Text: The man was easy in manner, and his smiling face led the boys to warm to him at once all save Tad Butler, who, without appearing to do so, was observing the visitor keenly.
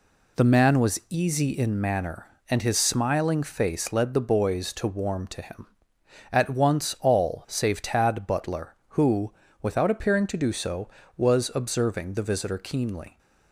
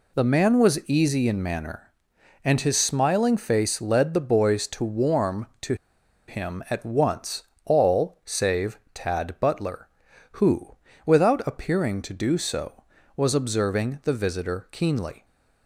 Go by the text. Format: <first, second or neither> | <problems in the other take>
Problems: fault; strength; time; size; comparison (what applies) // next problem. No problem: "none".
first | pauses between "to" and "him"; noticeable; at 5.7 s; 0.53 s long // pauses between "once" and "all"; slight; at 7.4 s; 0.22 s long // pauses between "save" and "Tad"; slight; at 8.7 s; 0.16 s long